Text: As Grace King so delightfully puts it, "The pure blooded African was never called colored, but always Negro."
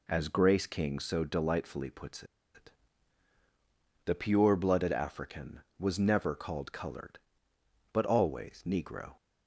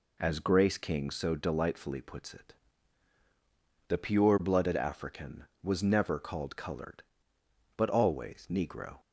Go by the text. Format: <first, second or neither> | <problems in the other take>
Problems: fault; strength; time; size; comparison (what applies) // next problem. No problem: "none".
second | pauses between "puts" and "it"; slight; at 2.2 s; 0.31 s long